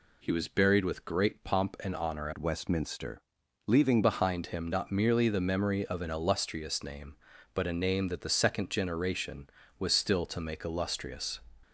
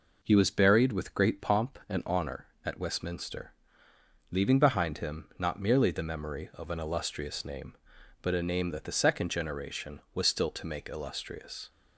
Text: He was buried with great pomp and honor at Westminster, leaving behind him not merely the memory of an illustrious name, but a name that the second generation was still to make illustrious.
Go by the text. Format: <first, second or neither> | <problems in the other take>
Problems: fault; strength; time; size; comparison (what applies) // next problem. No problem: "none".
second | changes voice from "at" to "leaving"; from 2.3 to 4.0 s; 1.7 s long